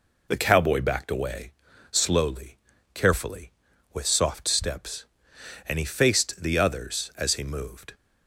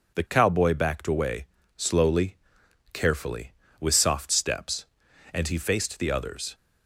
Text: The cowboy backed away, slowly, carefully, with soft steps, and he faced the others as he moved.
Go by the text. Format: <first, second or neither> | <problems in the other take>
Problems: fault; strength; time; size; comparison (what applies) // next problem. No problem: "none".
first | stops before "as he moved"; at 6.5 s